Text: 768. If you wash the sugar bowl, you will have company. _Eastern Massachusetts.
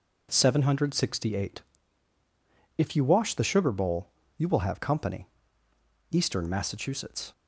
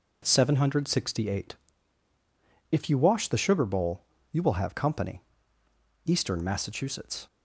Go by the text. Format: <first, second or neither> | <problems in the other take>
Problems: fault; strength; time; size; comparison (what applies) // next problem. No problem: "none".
neither | none